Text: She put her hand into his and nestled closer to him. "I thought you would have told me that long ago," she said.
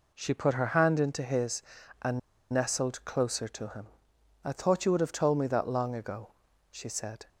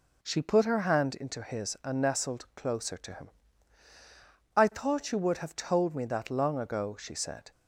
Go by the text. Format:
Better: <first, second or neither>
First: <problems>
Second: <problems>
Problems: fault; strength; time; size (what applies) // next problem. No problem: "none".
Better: second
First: pauses between "and" and "nestled"; slight; at 2.1 s; 0.33 s long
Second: none